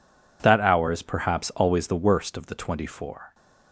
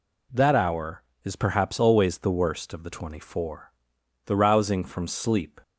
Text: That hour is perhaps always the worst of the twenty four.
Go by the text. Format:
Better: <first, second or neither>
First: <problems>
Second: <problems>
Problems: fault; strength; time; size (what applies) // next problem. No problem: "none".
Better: first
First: none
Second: goes on to say "The rousing from sleep"; from 4.2 s on; 1.3 s long